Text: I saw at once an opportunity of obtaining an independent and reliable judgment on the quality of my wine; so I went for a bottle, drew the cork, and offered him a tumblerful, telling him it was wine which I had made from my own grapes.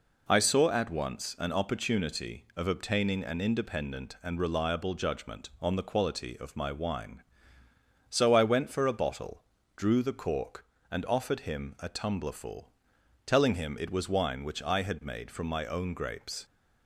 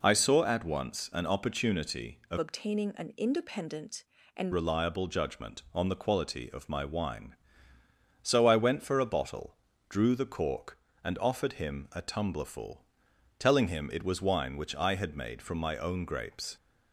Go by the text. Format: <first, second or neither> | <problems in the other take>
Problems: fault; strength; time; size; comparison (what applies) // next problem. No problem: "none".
first | changes voice from "obtaining" to "and"; from 2.3 to 4.5 s; 2.2 s long